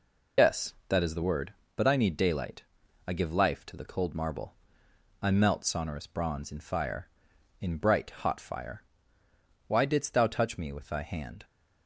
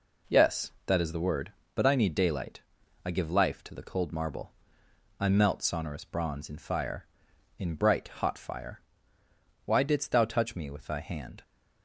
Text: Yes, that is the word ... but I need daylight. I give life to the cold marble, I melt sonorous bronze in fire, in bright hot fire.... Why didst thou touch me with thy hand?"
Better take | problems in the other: second | loses the start of "Yes"; at 0.3 s; 100 ms

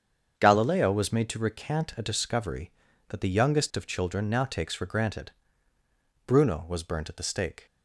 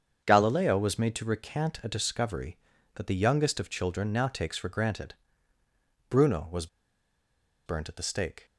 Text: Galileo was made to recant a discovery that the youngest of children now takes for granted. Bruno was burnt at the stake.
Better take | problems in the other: first | starts louder than the rest; strong; until 1.2 s; 7 dB; strong in the first // pauses between "was" and "burnt"; at 6.6 s; 0.99 s long

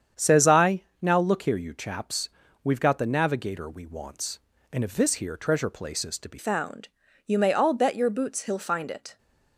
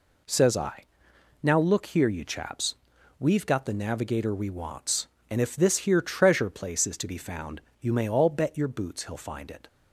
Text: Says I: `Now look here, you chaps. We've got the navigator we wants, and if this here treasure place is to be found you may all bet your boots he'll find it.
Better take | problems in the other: second | starts louder than the rest; strong; until 1.3 s; 8 dB // changes voice at "found"; from 6.3 s on; 2.8 s long // pauses between "found" and "you"; at 6.8 s; 0.38 s long; slight in the second

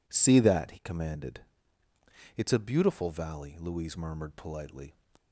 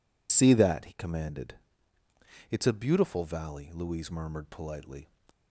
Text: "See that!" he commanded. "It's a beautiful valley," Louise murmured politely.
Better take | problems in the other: first | loses the start of "See"; at 0.2 s; 70 ms

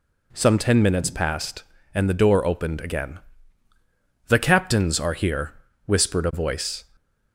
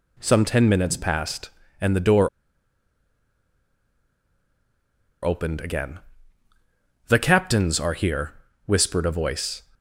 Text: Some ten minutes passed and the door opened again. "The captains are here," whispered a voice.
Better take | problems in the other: first | pauses between "door" and "opened"; strong; at 2.2 s; 2.9 s long

